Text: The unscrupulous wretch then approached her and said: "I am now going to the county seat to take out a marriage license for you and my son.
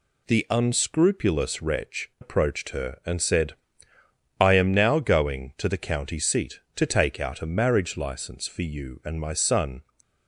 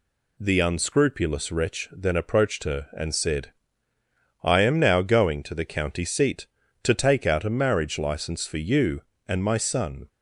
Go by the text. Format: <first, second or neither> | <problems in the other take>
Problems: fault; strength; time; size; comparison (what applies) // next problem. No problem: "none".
second | skips "then"; at 2.1 s